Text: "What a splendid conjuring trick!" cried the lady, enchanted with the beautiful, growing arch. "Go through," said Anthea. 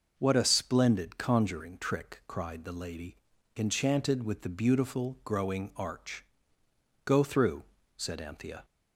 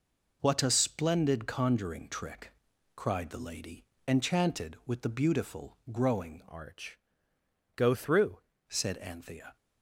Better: first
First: none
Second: changes voice from "arch" to "through"; from 6.4 to 8.4 s; 2.0 s long

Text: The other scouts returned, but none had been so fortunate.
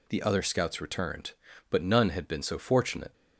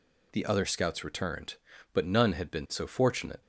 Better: neither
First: none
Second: none

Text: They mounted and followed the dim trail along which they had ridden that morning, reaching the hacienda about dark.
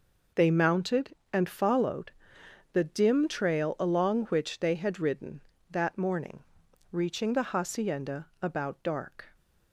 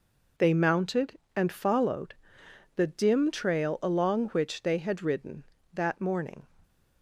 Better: first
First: pauses between "followed" and "the"; noticeable; at 2.1 s; 0.60 s long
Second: pauses between "followed" and "the"; noticeable; at 2.1 s; 0.60 s long // stops before "reaching the hacienda about dark"; at 6.6 s

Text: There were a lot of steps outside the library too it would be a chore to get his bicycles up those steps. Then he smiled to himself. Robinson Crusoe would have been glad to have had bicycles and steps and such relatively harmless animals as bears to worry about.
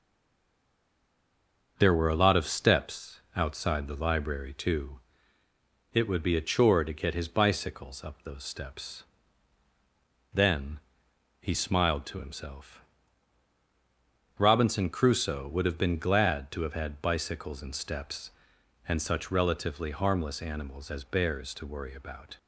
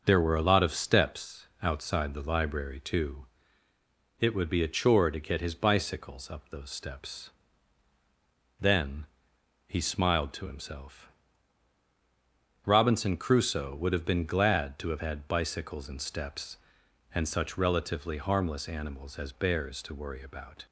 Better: second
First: stays silent before the first word; noticeable; until 1.7 s; 1.7 s long // starts louder than the rest; until 2.7 s; 6.5 dB // pauses between "steps" and "outside"; slight; at 3.1 s; 0.16 s long // pauses between "too" and "it"; noticeable; at 4.9 s; 0.94 s long // pauses between "Then" and "he"; noticeable; at 10.7 s; 0.60 s long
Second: starts louder than the rest; until 1.0 s; 6.5 dB // pauses between "steps" and "outside"; slight; at 1.4 s; 0.16 s long // pauses between "too" and "it"; noticeable; at 3.2 s; 0.94 s long // pauses between "Then" and "he"; noticeable; at 9.0 s; 0.60 s long

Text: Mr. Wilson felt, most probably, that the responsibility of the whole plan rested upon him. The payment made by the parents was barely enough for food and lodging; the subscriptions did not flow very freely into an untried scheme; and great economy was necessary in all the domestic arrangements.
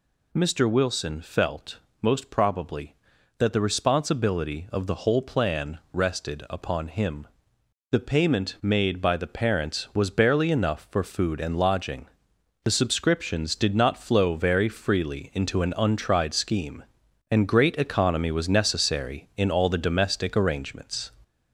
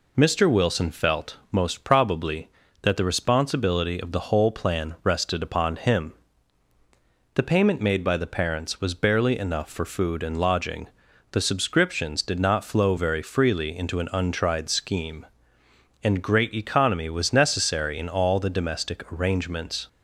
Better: second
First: gets louder; noticeable; throughout; 4 dB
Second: none

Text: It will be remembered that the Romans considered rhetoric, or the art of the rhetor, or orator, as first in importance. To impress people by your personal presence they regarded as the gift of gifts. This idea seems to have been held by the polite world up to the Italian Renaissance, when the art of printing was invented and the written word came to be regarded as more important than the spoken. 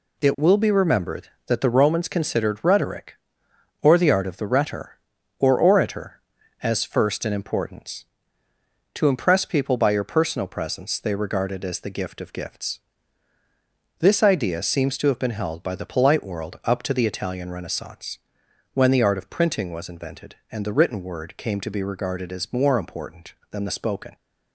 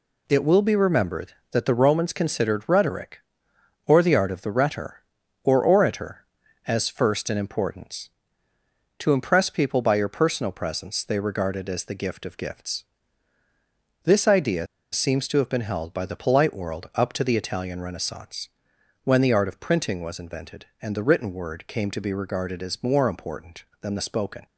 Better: first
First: none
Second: pauses between "idea" and "seems"; slight; at 14.6 s; 0.27 s long

